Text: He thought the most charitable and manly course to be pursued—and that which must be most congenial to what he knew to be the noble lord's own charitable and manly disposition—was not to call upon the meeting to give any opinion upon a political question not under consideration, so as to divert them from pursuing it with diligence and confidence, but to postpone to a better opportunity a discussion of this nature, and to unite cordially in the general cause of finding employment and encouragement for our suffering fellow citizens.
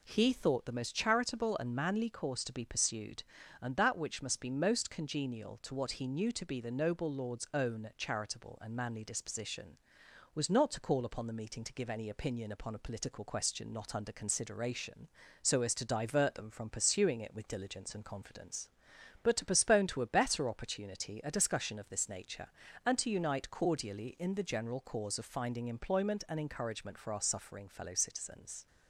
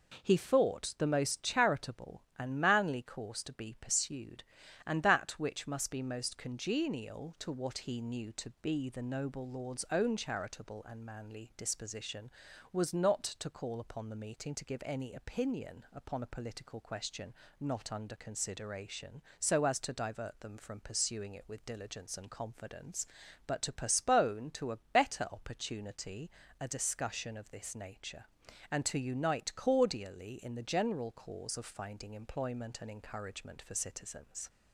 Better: first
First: none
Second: pauses between "question" and "not"; slight; at 17.3 s; 0.28 s long // pauses between "opportunity" and "a"; slight; at 26.3 s; 0.28 s long // skips "our suffering fellow"; at 33.7 s

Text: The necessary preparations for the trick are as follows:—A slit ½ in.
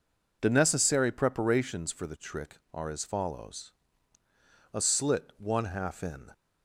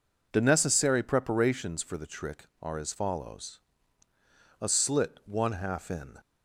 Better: neither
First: none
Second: none

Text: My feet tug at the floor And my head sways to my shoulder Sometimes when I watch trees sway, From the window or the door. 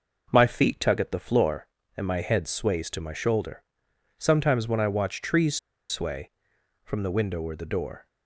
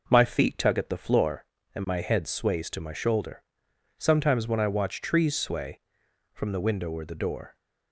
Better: second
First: pauses between "shoulder" and "Sometimes"; noticeable; at 3.6 s; 0.56 s long // pauses between "trees" and "sway"; slight; at 5.5 s; 0.33 s long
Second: pauses between "shoulder" and "Sometimes"; noticeable; at 3.4 s; 0.56 s long

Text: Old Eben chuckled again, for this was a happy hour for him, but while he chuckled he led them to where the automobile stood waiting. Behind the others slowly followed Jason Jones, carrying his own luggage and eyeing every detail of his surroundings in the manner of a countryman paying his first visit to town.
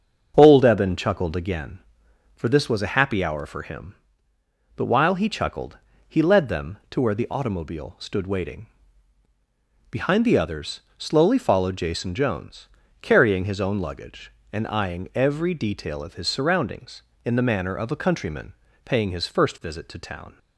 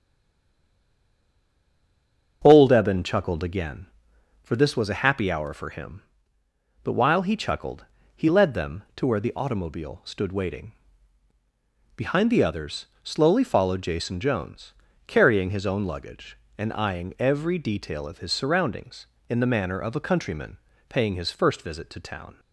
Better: first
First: starts louder than the rest; until 1.3 s; 6.5 dB // pauses between "chuckled" and "he"; slight; at 5.7 s; 0.32 s long // pauses between "others" and "slowly"; slight; at 10.8 s; 0.16 s long // pauses between "countryman" and "paying"; slight; at 18.5 s; 0.32 s long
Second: stays silent before the first word; until 2.4 s; 2.4 s long // starts louder than the rest; until 3.4 s; 6.5 dB // pauses between "chuckled" and "he"; slight; at 7.8 s; 0.32 s long // pauses between "others" and "slowly"; slight; at 12.8 s; 0.16 s long // pauses between "countryman" and "paying"; slight; at 20.5 s; 0.32 s long

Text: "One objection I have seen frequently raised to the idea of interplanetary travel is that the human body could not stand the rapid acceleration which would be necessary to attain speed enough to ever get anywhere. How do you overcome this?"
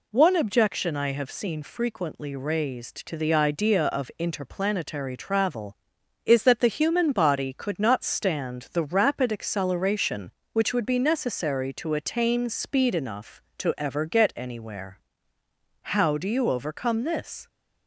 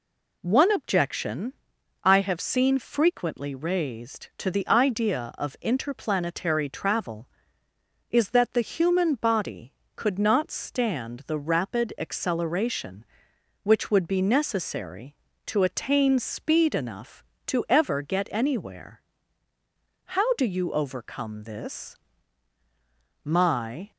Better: first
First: none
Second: pauses between "objection" and "I"; noticeable; at 1.5 s; 0.50 s long // goes on to say "My"; noticeable; from 23.2 s on; 0.66 s long

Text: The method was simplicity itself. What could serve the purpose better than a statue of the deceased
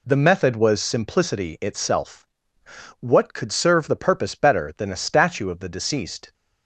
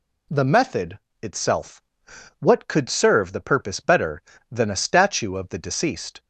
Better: first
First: none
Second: skips "was simplicity"; at 1.0 s

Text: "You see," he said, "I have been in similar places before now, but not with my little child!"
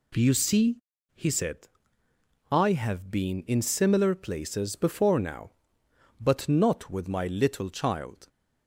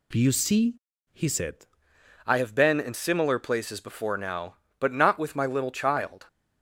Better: first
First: none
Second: changes voice at "I"; from 2.2 s on; 4.0 s long

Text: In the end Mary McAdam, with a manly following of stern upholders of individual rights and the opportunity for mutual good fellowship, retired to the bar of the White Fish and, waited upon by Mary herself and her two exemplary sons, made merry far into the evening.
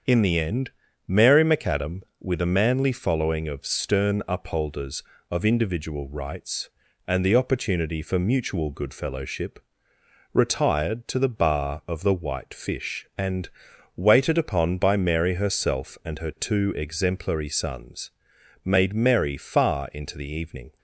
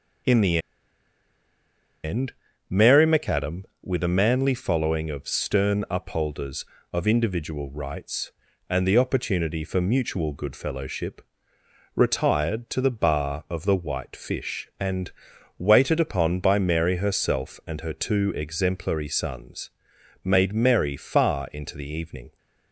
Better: first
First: starts louder than the rest; until 1.4 s; 7 dB // pauses between "end" and "Mary"; slight; at 0.7 s; 0.36 s long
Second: starts louder than the rest; until 3.0 s; 7 dB // pauses between "the" and "end"; strong; at 0.5 s; 1.4 s long // pauses between "end" and "Mary"; slight; at 2.3 s; 0.36 s long

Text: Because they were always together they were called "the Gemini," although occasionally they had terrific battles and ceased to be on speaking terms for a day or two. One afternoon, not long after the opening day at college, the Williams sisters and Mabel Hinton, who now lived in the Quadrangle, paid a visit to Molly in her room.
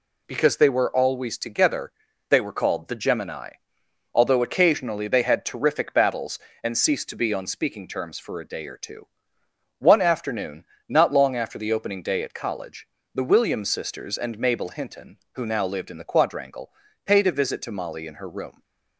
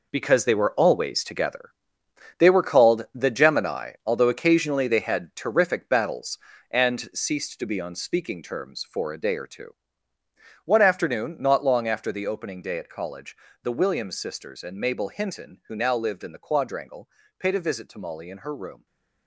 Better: first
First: pauses between "together" and "they"; at 1.9 s; 0.40 s long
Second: gets quieter; strong; throughout; 11 dB // pauses between "together" and "they"; noticeable; at 1.7 s; 0.68 s long // stays silent after the last word; slight; from 18.7 s on; 0.5 s long

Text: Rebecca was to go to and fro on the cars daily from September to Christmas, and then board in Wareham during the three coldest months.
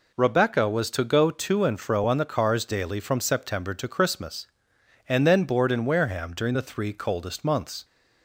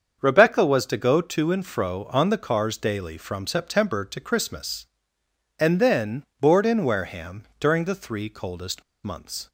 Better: first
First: none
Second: starts louder than the rest; until 1.2 s; 7 dB // pauses between "then" and "board"; slight; at 6.2 s; 0.16 s long // pauses between "Wareham" and "during"; slight; at 7.4 s; 0.16 s long // pauses between "coldest" and "months"; slight; at 8.8 s; 0.21 s long

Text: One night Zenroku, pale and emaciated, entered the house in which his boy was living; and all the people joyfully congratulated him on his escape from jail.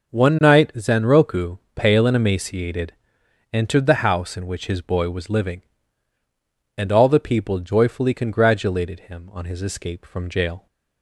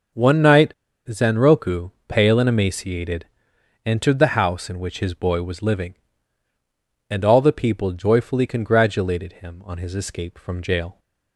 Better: first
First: none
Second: pauses between "night" and "Zenroku"; slight; at 0.7 s; 0.32 s long

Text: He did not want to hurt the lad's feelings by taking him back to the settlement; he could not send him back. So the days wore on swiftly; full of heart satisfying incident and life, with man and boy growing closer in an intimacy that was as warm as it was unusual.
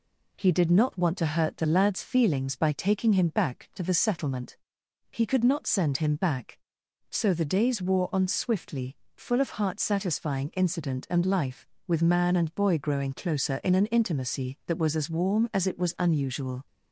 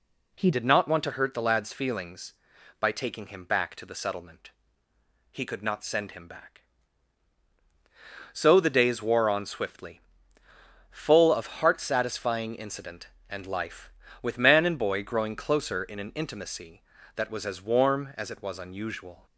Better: first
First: none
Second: changes voice at "did"; from 0.5 s on; 18.7 s long

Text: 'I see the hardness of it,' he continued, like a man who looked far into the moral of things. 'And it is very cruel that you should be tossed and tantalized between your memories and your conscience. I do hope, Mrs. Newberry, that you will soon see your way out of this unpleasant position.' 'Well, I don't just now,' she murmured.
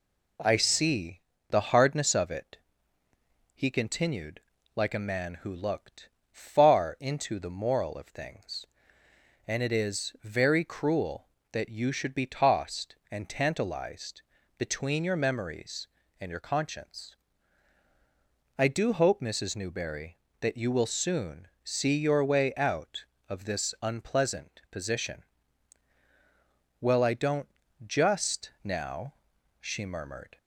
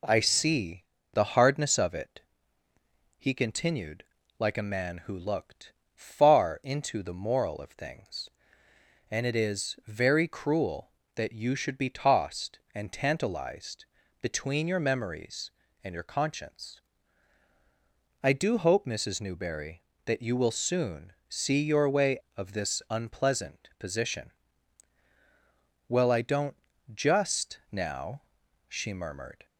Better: first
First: pauses between "see" and "the"; slight; at 1.1 s; 0.32 s long // pauses between "looked" and "far"; slight; at 6.0 s; 0.22 s long // pauses between "tantalized" and "between"; slight; at 14.2 s; 0.34 s long // pauses between "soon" and "see"; slight; at 21.4 s; 0.16 s long // pauses between "don't" and "just"; slight; at 27.4 s; 0.36 s long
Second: pauses between "see" and "the"; slight; at 0.8 s; 0.32 s long // pauses between "looked" and "far"; slight; at 5.7 s; 0.22 s long // pauses between "tantalized" and "between"; slight; at 13.8 s; 0.34 s long // pauses between "soon" and "see"; slight; at 21.1 s; 0.16 s long // skips "out"; at 22.2 s // pauses between "don't" and "just"; slight; at 26.5 s; 0.36 s long

